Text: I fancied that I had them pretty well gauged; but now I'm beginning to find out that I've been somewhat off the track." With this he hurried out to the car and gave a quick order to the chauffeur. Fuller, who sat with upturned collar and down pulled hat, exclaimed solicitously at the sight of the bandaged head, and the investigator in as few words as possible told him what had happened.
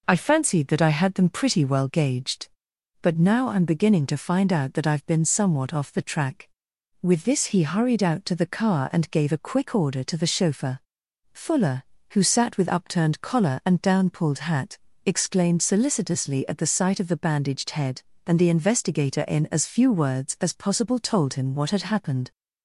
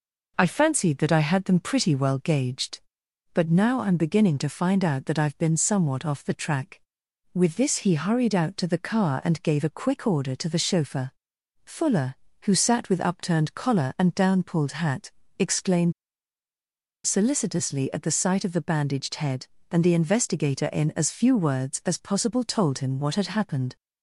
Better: first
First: none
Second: pauses between "exclaimed" and "solicitously"; at 15.9 s; 1.1 s long

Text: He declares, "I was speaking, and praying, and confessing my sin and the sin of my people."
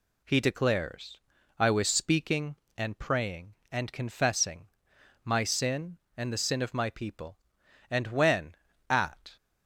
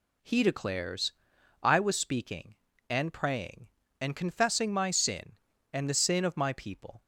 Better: second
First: pauses between "confessing" and "my"; noticeable; at 4.6 s; 0.56 s long // goes on to say "And when at"; from 7.9 s on; 1.4 s long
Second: none

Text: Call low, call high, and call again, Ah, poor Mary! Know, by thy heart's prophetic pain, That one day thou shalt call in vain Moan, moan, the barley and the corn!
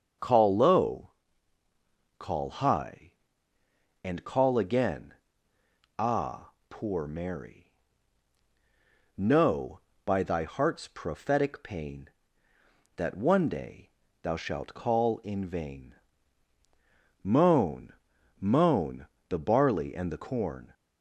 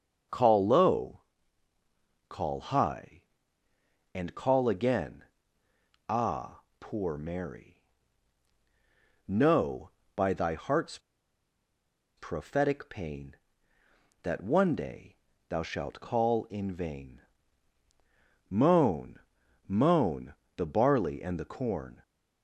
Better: first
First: starts louder than the rest; until 2.2 s; 6.5 dB // pauses between "day" and "thou"; slight; at 13.8 s; 0.32 s long // pauses between "vain" and "Moan"; strong; at 15.9 s; 1.2 s long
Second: starts louder than the rest; until 2.3 s; 6.5 dB // pauses between "heart's" and "prophetic"; at 10.9 s; 1.1 s long // pauses between "day" and "thou"; slight; at 15.1 s; 0.32 s long // pauses between "vain" and "Moan"; strong; at 17.2 s; 1.2 s long

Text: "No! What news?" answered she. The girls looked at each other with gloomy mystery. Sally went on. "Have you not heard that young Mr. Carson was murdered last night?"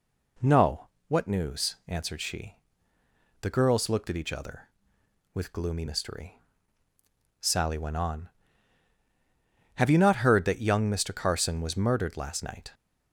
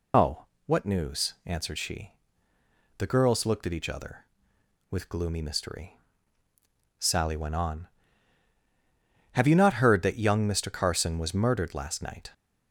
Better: first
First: none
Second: loses the start of "No"; at 0.1 s; 190 ms

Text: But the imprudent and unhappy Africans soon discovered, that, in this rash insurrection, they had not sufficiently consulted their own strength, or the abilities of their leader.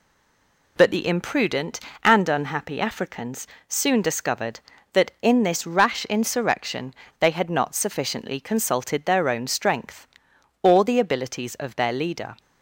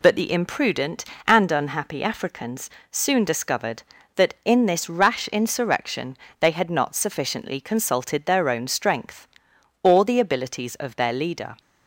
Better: second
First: stays silent before the first word; slight; until 0.7 s; 0.7 s long // pauses between "Africans" and "soon"; slight; at 3.4 s; 0.20 s long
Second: pauses between "Africans" and "soon"; slight; at 2.6 s; 0.20 s long

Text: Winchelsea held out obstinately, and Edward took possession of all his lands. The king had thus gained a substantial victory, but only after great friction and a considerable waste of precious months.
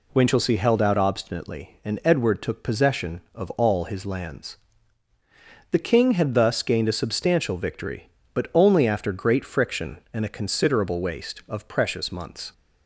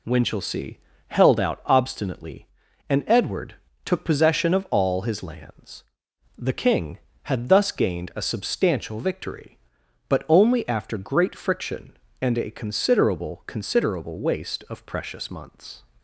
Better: first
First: none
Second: pauses between "Winchelsea" and "held"; slight; at 0.7 s; 0.30 s long // pauses between "Edward" and "took"; slight; at 3.5 s; 0.28 s long // says "considerable" twice; at 13.4 s

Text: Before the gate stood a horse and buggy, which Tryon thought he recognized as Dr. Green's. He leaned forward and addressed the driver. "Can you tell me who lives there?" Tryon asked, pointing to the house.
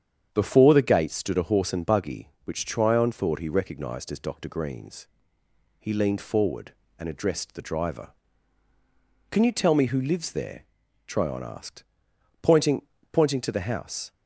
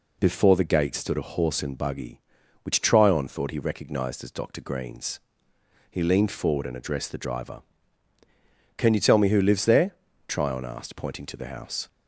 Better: second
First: starts louder than the rest; strong; until 1.3 s; 8 dB // says "pointing" twice; at 13.1 s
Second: none

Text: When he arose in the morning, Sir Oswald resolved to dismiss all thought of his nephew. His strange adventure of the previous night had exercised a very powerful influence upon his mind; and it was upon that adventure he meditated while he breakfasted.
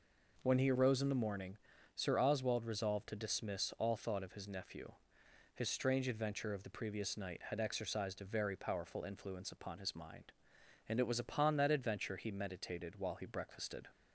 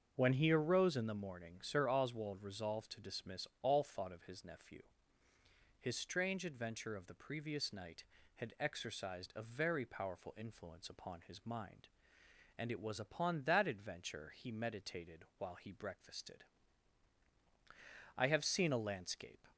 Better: first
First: none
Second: starts louder than the rest; until 1.1 s; 6.5 dB // goes on to say "I have seen a landscape"; noticeable; from 18.1 s on; 1.3 s long

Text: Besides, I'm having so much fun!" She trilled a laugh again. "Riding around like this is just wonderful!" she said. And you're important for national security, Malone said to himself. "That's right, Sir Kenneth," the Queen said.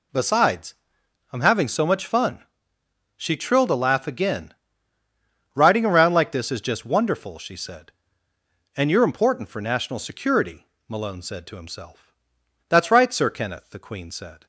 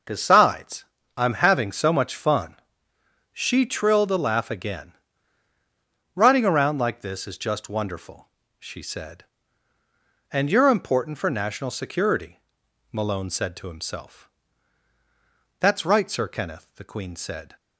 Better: neither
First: none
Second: none

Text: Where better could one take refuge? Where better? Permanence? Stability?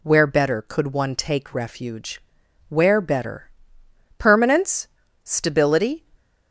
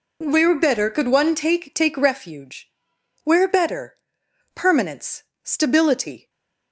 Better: first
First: none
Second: says "take" twice; at 1.7 s // stays silent after the last word; slight; from 6.1 s on; 0.6 s long

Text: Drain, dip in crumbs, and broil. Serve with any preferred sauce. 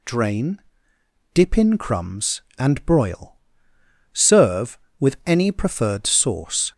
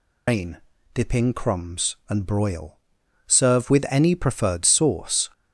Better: first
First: none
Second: loses the start of "Drain"; at 0.2 s; 155 ms

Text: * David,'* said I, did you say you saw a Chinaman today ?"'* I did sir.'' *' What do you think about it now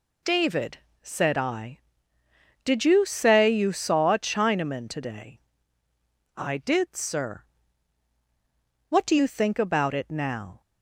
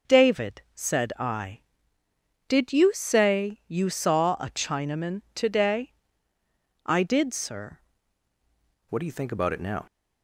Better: first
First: none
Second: starts louder than the rest; until 1.2 s; 6.5 dB // changes voice at "What"; from 8.8 s on; 1.0 s long

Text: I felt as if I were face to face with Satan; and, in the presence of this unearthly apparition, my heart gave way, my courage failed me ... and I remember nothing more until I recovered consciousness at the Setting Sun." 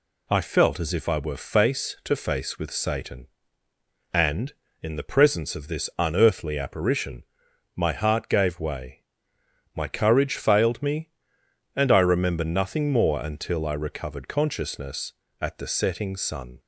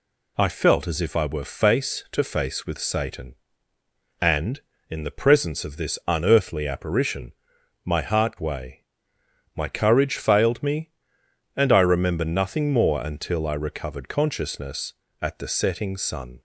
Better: first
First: none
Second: skips "gave"; at 8.3 s

